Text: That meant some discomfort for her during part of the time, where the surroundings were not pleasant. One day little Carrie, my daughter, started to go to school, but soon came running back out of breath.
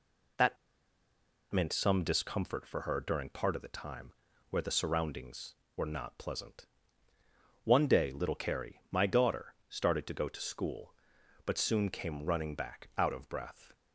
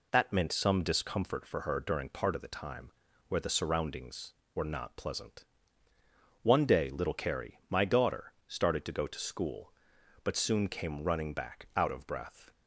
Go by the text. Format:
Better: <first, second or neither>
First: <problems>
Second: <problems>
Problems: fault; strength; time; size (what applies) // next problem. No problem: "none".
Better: second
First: pauses between "That" and "meant"; noticeable; at 0.5 s; 0.95 s long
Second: none